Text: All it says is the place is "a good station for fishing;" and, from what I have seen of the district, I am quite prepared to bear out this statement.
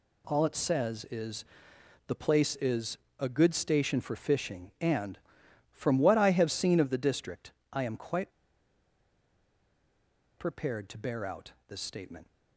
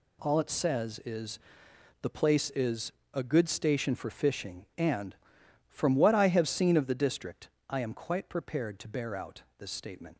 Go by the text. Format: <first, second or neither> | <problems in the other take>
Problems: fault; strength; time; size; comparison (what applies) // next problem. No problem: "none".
second | pauses between "is" and "the"; noticeable; at 1.4 s; 0.64 s long; noticeable in the second // pauses between "is" and "a"; slight; at 2.9 s; 0.22 s long; slight in the second // pauses between "quite" and "prepared"; strong; at 8.3 s; 2.0 s long // pauses between "out" and "this"; slight; at 11.5 s; 0.16 s long; slight in the second